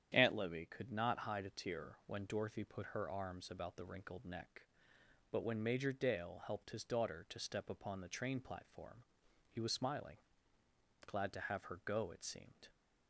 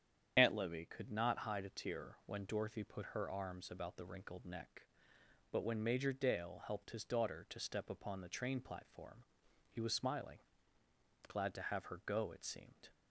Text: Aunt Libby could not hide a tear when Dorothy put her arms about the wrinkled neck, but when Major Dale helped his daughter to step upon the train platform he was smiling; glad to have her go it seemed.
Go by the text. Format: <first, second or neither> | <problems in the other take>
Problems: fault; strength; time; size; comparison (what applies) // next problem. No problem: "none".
first | loses the start of "Aunt"; at 0.3 s; 55 ms // starts louder than the rest; strong; until 1.3 s; 9 dB; strong in the first // pauses between "platform" and "he"; at 9.2 s; 0.44 s long; also in the first